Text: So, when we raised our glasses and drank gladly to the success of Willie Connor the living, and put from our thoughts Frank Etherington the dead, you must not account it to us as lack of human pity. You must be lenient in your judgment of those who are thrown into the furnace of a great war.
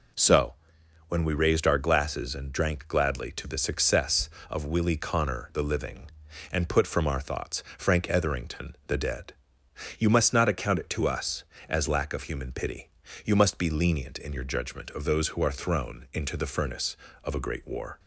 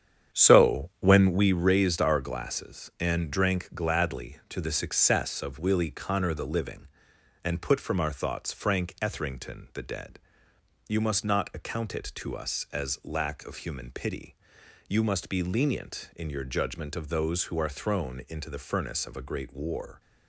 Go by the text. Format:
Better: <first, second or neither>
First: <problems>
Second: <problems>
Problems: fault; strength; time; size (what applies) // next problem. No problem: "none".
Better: first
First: none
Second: starts louder than the rest; strong; until 1.6 s; 8.5 dB